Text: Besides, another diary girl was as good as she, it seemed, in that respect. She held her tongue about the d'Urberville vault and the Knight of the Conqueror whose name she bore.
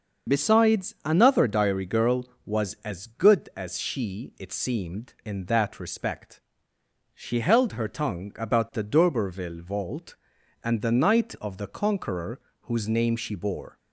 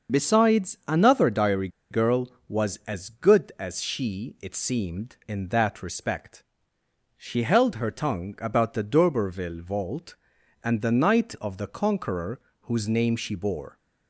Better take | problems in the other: first | starts louder than the rest; until 1.2 s; 6.5 dB; also in the first // pauses between "diary" and "girl"; slight; at 1.6 s; 0.22 s long // pauses between "Conqueror" and "whose"; slight; at 12.3 s; 0.22 s long; slight in the first

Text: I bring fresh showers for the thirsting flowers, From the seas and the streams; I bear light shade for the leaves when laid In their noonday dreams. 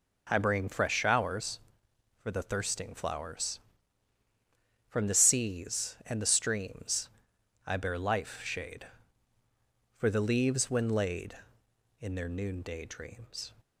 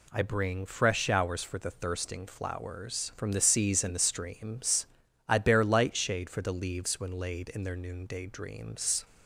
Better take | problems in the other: second | says "life" for "light"; at 7.9 s

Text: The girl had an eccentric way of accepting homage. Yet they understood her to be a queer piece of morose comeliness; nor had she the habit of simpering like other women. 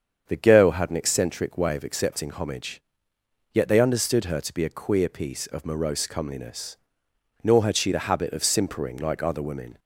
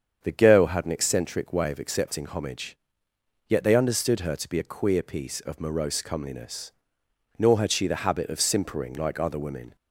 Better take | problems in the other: neither | starts louder than the rest; strong; the same in both

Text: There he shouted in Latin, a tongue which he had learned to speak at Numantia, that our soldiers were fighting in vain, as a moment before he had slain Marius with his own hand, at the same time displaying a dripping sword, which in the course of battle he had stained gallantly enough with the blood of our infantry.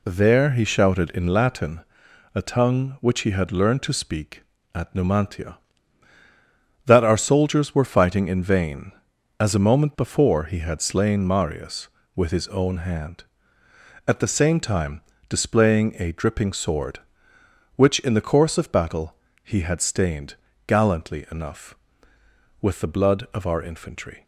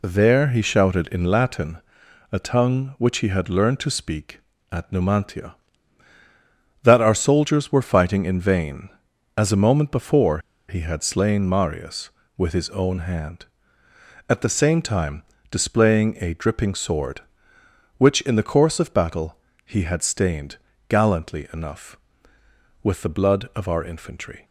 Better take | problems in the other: first | pauses between "before" and "he"; slight; at 10.3 s; 0.28 s long // pauses between "time" and "displaying"; slight; at 15.2 s; 0.26 s long; slight in the first // pauses between "battle" and "he"; slight; at 19.3 s; 0.30 s long; slight in the first // pauses between "stained" and "gallantly"; slight; at 20.5 s; 0.32 s long; slight in the first

